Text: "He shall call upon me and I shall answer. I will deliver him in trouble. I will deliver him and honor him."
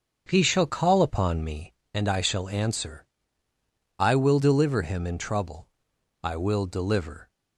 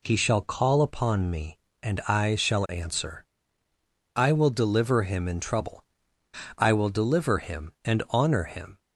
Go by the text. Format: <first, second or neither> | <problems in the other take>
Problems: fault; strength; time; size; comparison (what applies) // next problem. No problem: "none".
second | starts louder than the rest; until 1.3 s; 6.5 dB // stops before "him and honor him"; at 7.2 s